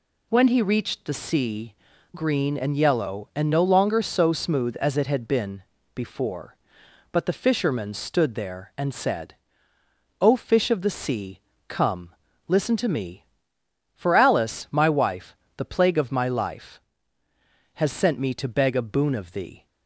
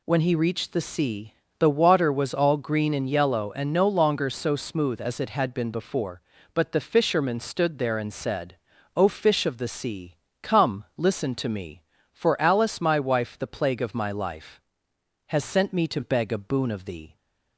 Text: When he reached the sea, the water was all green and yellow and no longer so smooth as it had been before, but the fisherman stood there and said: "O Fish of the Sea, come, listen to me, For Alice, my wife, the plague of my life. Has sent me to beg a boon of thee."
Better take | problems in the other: second | skips "the water was all"; at 1.9 s // pauses between "been" and "before"; slight; at 5.6 s; 0.32 s long

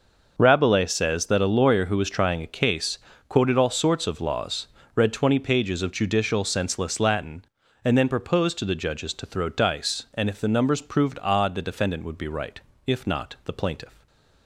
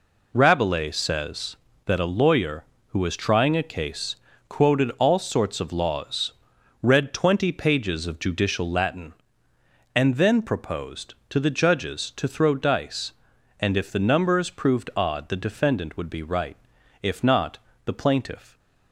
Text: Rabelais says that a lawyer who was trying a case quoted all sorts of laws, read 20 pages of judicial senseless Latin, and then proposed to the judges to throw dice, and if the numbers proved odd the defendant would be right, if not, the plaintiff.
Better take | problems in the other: first | pauses between "case" and "quoted"; slight; at 4.1 s; 0.32 s long; slight in the first // skips "senseless"; at 8.7 s

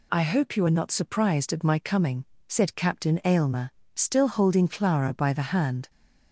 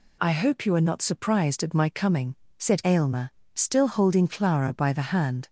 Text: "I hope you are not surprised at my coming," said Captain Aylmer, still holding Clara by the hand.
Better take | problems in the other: first | skips "Captain"; at 2.8 s

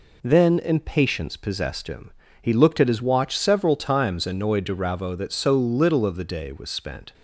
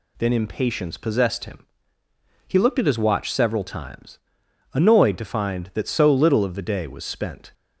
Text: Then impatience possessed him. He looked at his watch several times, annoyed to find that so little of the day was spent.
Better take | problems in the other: second | says "ravo" for "find"; at 4.7 s

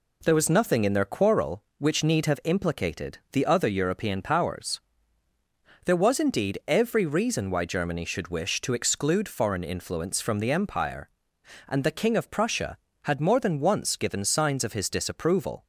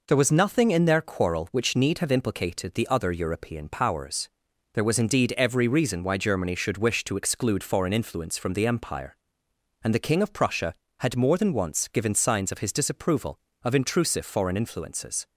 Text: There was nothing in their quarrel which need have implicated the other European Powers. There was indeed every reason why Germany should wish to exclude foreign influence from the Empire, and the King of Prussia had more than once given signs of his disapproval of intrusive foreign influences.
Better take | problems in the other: second | stops before "of intrusive foreign influences"; at 15.6 s

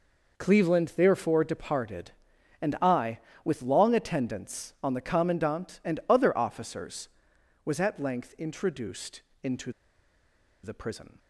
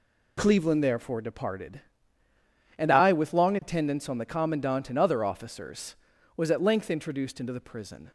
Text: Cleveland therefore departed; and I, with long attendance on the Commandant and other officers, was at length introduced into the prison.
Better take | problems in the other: second | pauses between "introduced" and "into"; slight; at 9.2 s; 0.22 s long // pauses between "into" and "the"; noticeable; at 9.7 s; 0.92 s long

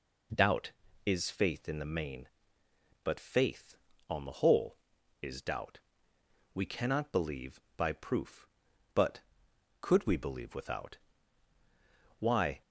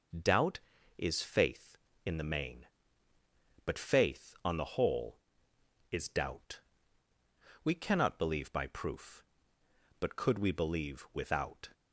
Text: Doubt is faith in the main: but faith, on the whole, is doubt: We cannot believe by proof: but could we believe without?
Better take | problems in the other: second | goes on to say "Why"; slight; from 12.1 s on; 0.42 s long

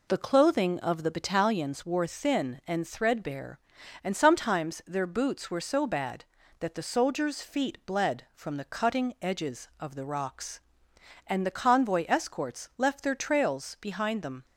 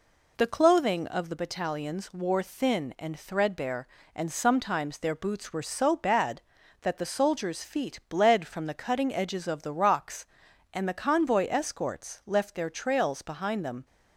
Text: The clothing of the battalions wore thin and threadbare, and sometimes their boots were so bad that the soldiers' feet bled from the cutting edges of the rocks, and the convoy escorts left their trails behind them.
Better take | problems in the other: neither | none

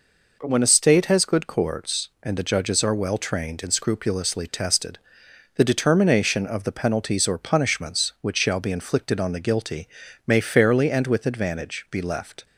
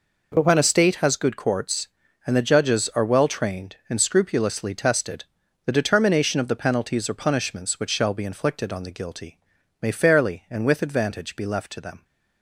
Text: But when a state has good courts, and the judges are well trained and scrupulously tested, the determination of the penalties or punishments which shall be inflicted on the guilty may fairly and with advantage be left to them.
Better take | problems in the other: second | pauses between "guilty" and "may"; at 9.8 s; 0.40 s long; also in the second // stops before "to them"; at 12.4 s

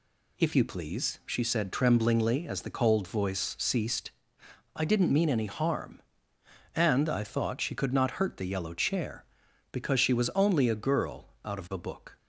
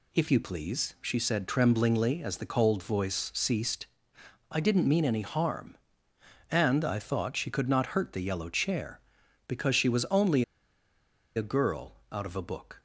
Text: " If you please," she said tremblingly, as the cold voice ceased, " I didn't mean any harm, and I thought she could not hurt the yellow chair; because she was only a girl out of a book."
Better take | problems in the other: first | pauses between "only" and "a"; noticeable; at 10.4 s; 0.91 s long

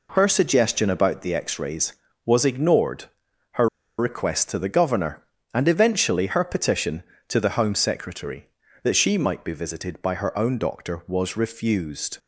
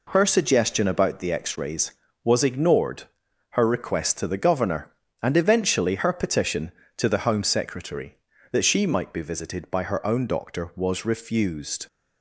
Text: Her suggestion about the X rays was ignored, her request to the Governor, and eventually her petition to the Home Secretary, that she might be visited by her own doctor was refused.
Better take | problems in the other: second | pauses between "her" and "request"; slight; at 3.6 s; 0.30 s long

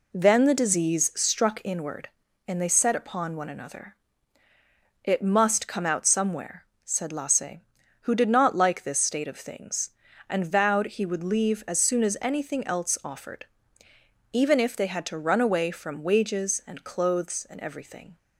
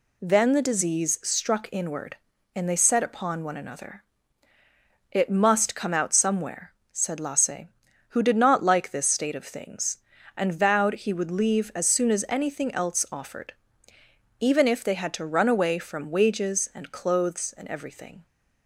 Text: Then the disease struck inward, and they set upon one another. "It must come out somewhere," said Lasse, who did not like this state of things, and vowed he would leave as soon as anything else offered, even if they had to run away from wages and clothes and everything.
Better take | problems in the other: second | starts louder than the rest; slight; until 1.7 s; 2.5 dB

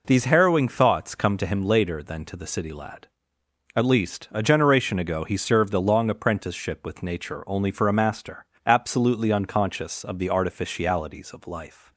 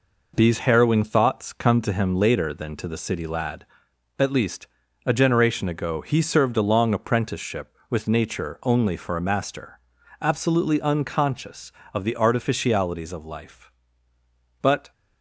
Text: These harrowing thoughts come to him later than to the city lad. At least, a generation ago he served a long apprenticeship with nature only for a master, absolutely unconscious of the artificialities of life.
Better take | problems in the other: first | goes on to say "But"; slight; from 14.6 s on; 0.30 s long

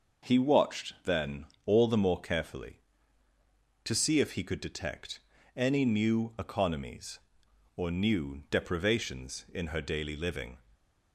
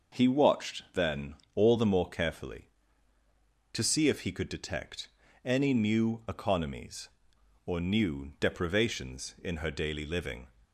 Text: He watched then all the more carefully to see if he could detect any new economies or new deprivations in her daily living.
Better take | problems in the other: neither | pauses between "then" and "all"; slight; the same in both // pauses between "detect" and "any"; slight; the same in both

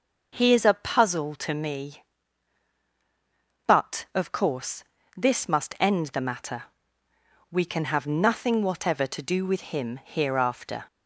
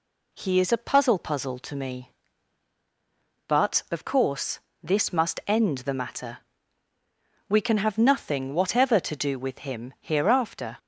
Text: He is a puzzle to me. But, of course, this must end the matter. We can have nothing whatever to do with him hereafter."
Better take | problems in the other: first | says "puzzle" twice; at 1.1 s

